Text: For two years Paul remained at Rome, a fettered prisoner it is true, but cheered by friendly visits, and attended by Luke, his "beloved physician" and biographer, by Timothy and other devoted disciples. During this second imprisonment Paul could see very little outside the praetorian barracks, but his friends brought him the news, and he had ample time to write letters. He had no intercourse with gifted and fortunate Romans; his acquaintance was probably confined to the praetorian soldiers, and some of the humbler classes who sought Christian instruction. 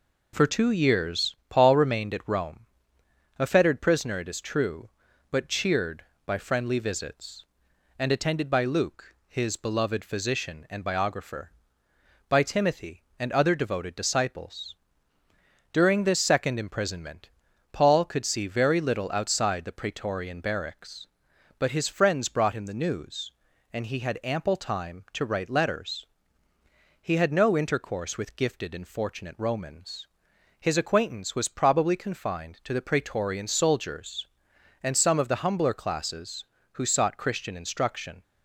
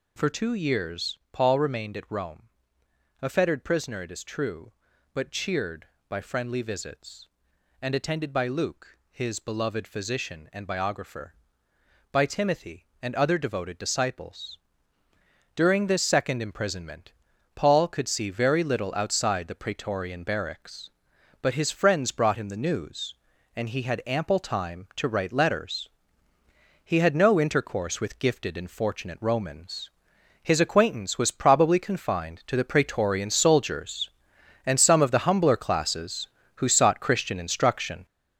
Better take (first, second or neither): first